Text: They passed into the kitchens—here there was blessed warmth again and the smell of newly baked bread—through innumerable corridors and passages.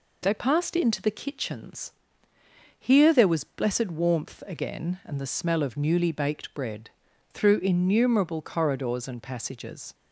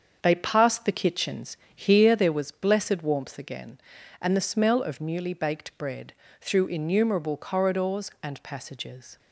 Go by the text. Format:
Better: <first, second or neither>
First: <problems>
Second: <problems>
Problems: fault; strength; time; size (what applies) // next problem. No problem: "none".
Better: first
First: none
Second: starts louder than the rest; until 1.2 s; 7 dB // skips "into"; at 0.8 s